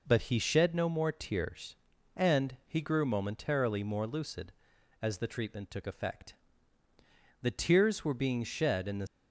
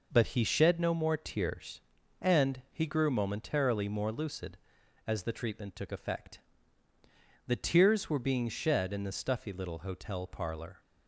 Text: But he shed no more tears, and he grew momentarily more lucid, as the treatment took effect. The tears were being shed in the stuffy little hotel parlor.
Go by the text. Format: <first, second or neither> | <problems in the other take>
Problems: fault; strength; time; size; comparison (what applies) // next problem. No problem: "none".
second | stops before "stuffy little hotel parlor"; at 9.0 s